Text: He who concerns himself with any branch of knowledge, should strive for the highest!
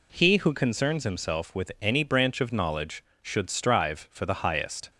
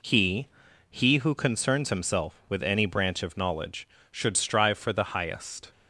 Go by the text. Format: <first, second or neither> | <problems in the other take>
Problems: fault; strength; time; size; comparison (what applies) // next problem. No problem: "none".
first | says "He" twice; at 0.9 s